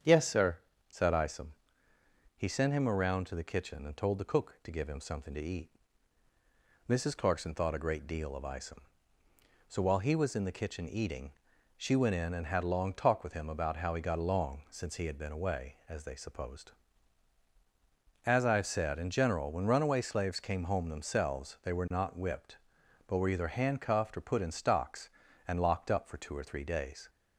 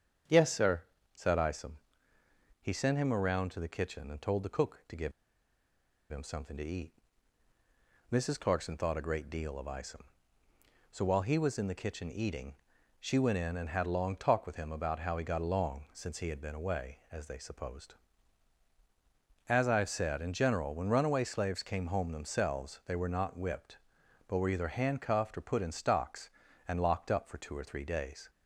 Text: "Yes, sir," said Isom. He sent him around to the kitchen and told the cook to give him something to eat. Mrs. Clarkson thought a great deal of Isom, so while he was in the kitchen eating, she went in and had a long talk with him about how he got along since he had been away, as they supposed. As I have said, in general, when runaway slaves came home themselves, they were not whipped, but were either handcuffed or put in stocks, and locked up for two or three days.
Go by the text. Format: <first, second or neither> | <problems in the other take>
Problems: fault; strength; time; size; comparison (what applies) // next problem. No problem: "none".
first | starts louder than the rest; strong; until 1.6 s; 8 dB; strong in the first // pauses between "give" and "him"; at 5.1 s; 0.99 s long